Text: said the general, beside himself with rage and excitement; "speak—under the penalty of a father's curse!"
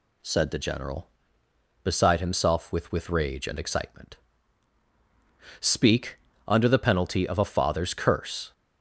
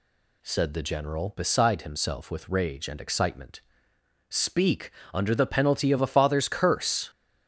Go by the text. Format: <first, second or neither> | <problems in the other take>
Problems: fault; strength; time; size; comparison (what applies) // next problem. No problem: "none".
second | says "with" twice; at 2.9 s